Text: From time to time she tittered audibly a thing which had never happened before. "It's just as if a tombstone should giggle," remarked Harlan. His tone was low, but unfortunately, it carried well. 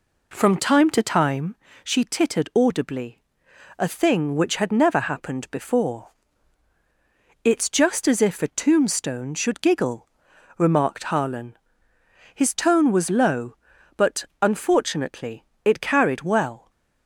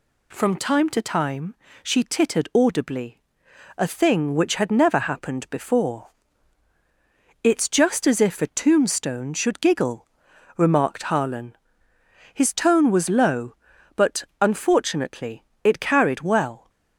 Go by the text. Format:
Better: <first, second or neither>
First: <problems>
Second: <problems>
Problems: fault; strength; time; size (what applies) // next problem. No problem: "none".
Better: second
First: starts louder than the rest; until 1.6 s; 3.5 dB // pauses between "time" and "she"; slight; at 1.5 s; 0.30 s long // pauses between "audibly" and "a"; noticeable; at 3.2 s; 0.58 s long // pauses between "but" and "unfortunately"; slight; at 14.2 s; 0.16 s long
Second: pauses between "time" and "she"; slight; at 1.5 s; 0.30 s long // pauses between "audibly" and "a"; noticeable; at 3.1 s; 0.58 s long // pauses between "but" and "unfortunately"; slight; at 14.2 s; 0.16 s long